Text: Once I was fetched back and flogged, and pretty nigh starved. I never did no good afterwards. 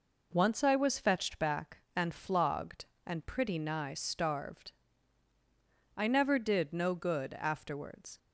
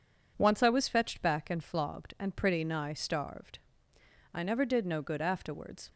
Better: neither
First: none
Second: none

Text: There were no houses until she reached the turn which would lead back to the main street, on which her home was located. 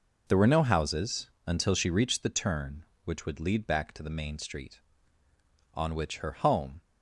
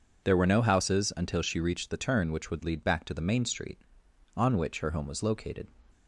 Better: second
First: pauses between "houses" and "until"; slight; at 1.2 s; 0.16 s long // stops before "was located"; at 6.7 s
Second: none

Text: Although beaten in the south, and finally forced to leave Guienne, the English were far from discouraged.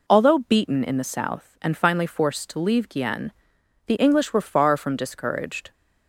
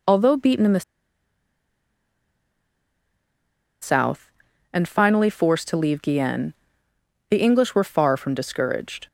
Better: first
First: none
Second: pauses between "the" and "south"; strong; at 0.8 s; 3.0 s long

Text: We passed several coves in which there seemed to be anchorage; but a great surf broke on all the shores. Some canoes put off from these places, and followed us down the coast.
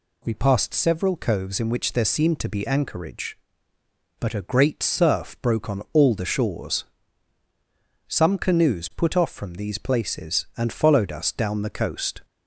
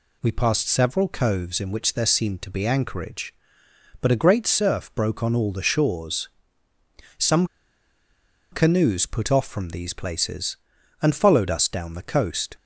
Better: first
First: none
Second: pauses between "Some" and "canoes"; at 7.4 s; 1.0 s long

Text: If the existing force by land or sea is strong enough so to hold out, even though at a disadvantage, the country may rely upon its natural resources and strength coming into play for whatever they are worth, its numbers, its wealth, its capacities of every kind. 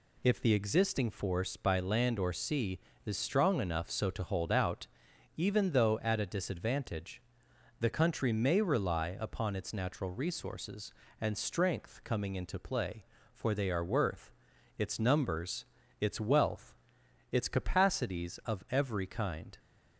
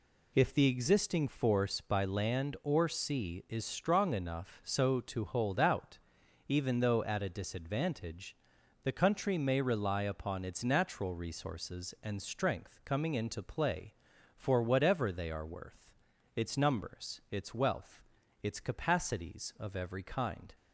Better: second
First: skips "whatever"; at 13.5 s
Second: none

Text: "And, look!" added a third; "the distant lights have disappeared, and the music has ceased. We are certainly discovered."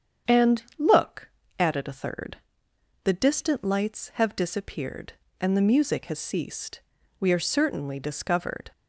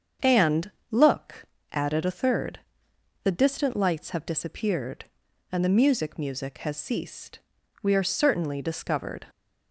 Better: first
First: starts louder than the rest; strong; until 1.7 s; 7.5 dB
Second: starts louder than the rest; strong; until 1.4 s; 7 dB // says "music" twice; at 6.1 s

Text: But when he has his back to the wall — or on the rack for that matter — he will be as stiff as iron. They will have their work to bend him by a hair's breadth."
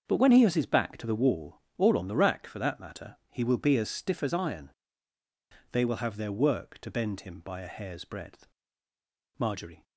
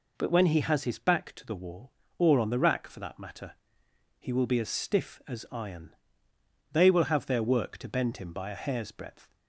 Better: second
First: starts louder than the rest; until 1.0 s; 6.5 dB // goes on to say "Marjorie"; slight; from 9.3 s on; 0.44 s long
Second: none

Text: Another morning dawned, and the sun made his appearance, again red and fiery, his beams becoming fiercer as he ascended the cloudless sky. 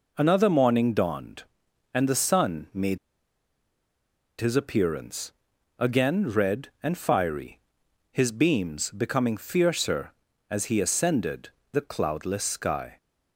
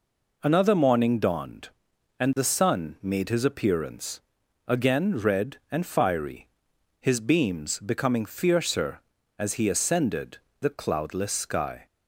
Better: second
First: pauses between "made" and "his"; strong; at 2.9 s; 1.4 s long // pauses between "ascended" and "the"; slight; at 11.4 s; 0.22 s long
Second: pauses between "ascended" and "the"; slight; at 10.3 s; 0.22 s long

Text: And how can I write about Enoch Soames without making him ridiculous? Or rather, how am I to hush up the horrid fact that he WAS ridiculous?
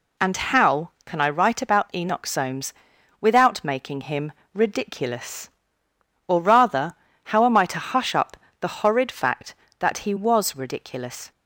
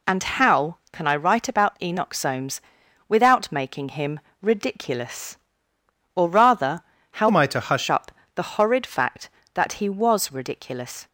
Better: first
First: pauses between "Soames" and "without"; noticeable; at 2.7 s; 0.48 s long // pauses between "him" and "ridiculous"; slight; at 4.3 s; 0.22 s long // pauses between "up" and "the"; slight; at 8.3 s; 0.24 s long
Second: pauses between "Soames" and "without"; noticeable; at 2.5 s; 0.48 s long // pauses between "him" and "ridiculous"; slight; at 4.1 s; 0.22 s long // changes voice from "am" to "hush"; from 7.2 to 7.8 s; 0.6 s long // pauses between "up" and "the"; slight; at 8.1 s; 0.24 s long

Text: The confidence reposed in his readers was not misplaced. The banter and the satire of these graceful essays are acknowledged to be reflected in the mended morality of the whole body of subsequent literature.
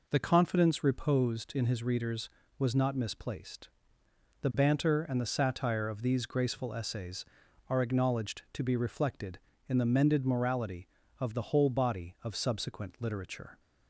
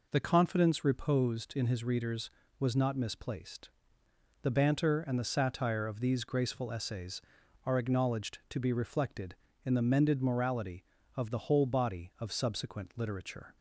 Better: neither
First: none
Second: none

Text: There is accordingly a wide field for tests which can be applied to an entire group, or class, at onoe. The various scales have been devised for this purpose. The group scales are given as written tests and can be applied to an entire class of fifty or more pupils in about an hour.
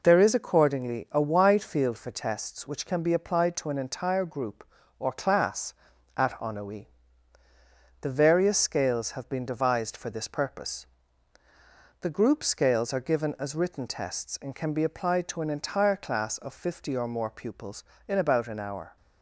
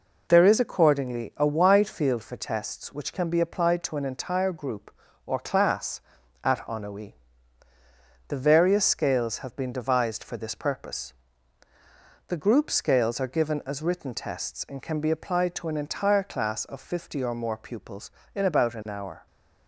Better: neither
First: none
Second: none

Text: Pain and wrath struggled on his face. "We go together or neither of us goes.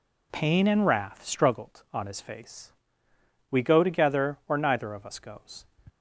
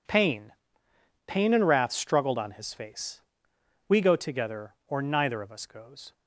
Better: first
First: none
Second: says "Pain" twice; at 1.2 s

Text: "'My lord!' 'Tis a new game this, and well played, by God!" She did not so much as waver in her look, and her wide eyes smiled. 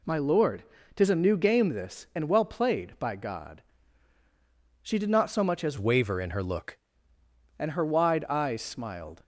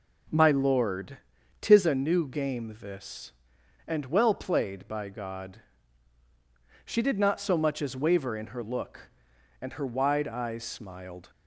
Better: second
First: changes voice from "waver" to "look"; from 5.7 to 6.7 s; 1.0 s long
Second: none

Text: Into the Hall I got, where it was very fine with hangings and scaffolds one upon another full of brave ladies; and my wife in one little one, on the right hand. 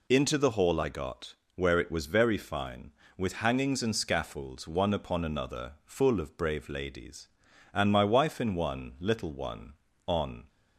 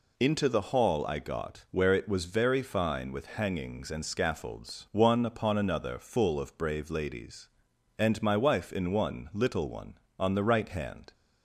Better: second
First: stops before "the right hand"; at 10.4 s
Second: none

